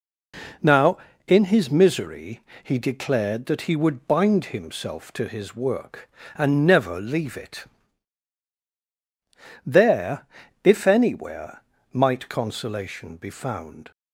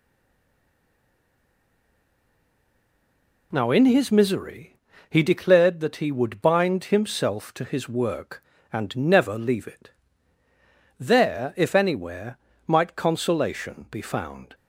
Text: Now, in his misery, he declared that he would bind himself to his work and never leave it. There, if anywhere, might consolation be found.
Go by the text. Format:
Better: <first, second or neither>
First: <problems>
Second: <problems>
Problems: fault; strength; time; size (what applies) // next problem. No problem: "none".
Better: first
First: none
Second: stays silent before the first word; strong; until 3.5 s; 3.5 s long